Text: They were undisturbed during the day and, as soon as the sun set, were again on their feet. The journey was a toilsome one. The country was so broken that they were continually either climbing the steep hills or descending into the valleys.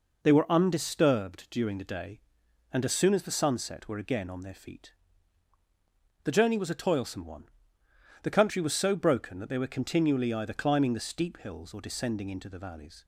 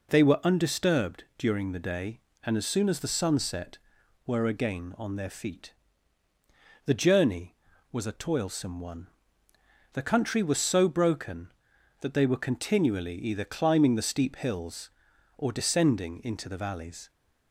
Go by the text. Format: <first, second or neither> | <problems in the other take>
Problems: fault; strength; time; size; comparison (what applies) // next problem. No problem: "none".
neither | none